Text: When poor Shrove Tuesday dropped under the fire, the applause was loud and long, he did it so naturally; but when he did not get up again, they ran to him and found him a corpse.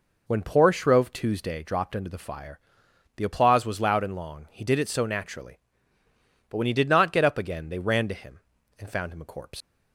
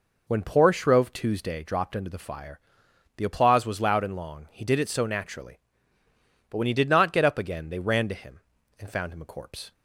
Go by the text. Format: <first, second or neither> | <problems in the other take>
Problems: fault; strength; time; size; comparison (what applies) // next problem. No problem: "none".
second | leaves "corpse" unfinished; at 9.6 s; 110 ms